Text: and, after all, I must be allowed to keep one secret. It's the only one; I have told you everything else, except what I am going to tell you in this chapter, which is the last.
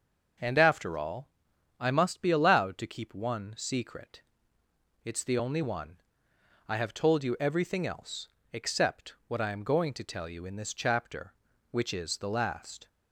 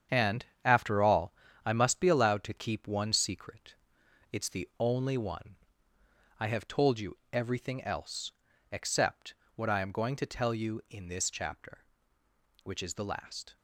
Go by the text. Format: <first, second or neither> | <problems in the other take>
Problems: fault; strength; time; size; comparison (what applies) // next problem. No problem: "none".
first | gets quieter; strong; throughout; 8 dB // starts louder than the rest; strong; until 1.2 s; 8 dB; also in the first // pauses between "you" and "everything"; slight; at 7.1 s; 0.16 s long // pauses between "except" and "what"; slight; at 9.3 s; 0.22 s long